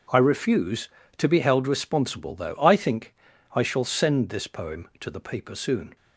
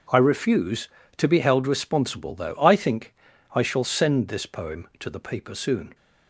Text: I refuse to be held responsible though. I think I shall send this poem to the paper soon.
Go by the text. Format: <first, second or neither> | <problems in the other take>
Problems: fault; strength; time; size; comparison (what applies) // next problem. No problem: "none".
neither | pauses between "think" and "I"; the same in both